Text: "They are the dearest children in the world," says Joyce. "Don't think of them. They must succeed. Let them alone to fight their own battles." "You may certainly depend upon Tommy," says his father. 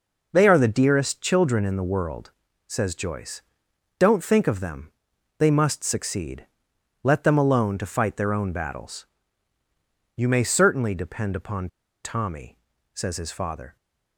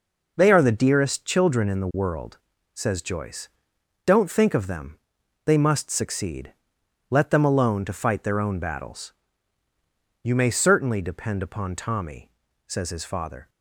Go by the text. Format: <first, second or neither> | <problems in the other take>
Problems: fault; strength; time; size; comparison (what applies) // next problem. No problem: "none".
second | pauses between "upon" and "Tommy"; slight; at 11.6 s; 0.35 s long